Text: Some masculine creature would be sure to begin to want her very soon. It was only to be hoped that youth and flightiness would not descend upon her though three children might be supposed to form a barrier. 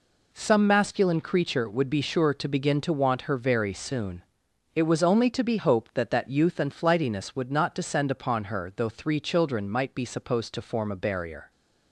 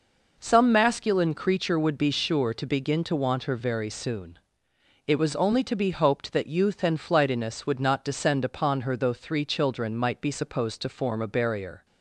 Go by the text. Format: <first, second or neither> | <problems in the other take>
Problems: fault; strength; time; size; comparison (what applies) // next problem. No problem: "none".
second | says "that" twice; at 6.1 s